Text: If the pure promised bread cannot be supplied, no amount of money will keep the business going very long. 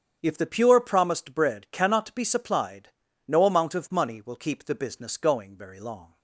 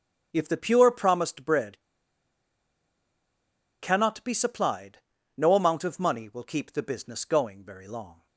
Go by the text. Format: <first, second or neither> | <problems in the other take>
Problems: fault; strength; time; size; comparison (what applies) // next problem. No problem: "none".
first | starts louder than the rest; strong; until 1.3 s; 8.5 dB; strong in the first // pauses between "bread" and "cannot"; strong; at 1.7 s; 2.0 s long